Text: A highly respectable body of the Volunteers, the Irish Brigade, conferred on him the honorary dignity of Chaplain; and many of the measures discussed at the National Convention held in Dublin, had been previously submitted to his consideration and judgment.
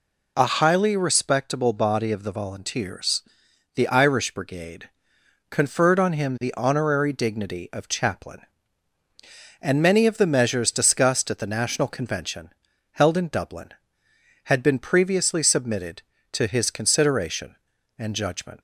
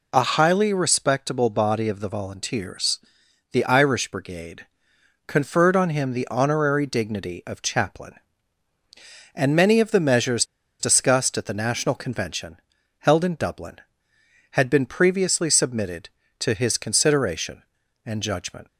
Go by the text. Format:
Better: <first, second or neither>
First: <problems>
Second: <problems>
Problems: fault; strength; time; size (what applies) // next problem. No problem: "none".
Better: first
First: pauses between "Convention" and "held"; at 12.4 s; 0.44 s long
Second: pauses between "measures" and "discussed"; slight; at 10.4 s; 0.34 s long // pauses between "Convention" and "held"; at 12.5 s; 0.44 s long